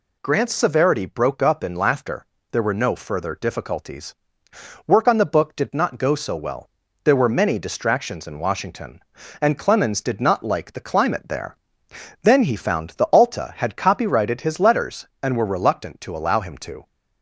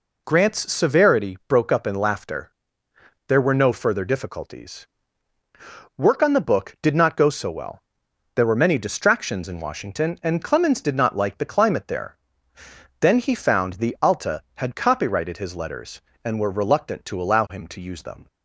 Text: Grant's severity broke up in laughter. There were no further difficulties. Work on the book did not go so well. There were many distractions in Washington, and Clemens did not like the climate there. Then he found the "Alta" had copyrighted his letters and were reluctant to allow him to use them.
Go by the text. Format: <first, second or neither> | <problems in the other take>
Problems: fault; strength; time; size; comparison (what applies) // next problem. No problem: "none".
second | stops before "use them"; at 16.8 s